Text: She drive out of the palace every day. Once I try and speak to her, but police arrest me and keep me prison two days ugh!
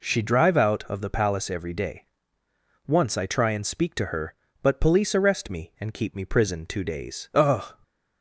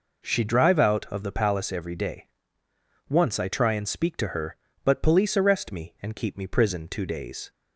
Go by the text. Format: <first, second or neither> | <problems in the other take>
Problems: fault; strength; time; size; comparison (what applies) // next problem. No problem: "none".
first | stops before "ugh"; at 7.5 s